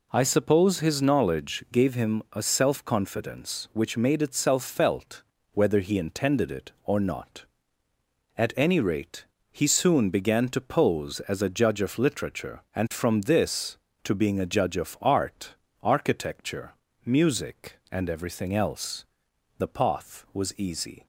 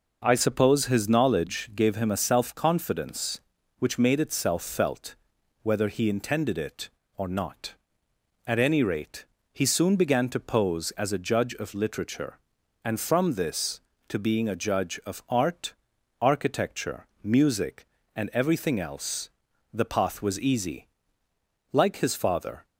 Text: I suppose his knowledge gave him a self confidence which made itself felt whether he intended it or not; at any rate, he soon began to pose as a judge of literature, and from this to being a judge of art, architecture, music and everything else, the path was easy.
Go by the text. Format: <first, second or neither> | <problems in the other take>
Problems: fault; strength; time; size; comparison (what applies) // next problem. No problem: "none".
first | pauses between "felt" and "whether"; noticeable; at 5.1 s; 0.46 s long; slight in the first // goes on to say "Like his father"; noticeable; from 21.7 s on; 0.94 s long